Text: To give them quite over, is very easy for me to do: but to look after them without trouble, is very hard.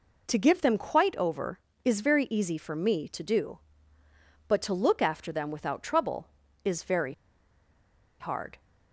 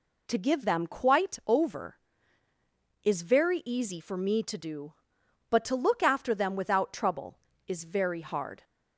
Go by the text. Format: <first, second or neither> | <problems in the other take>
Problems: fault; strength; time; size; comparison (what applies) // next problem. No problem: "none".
second | pauses between "very" and "hard"; at 7.1 s; 1.0 s long